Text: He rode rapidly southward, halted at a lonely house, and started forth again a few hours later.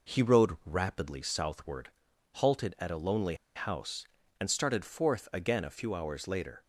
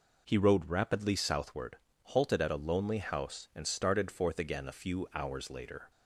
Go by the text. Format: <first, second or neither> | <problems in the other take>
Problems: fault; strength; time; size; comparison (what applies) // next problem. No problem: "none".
second | pauses between "lonely" and "house"; slight; at 3.3 s; 0.20 s long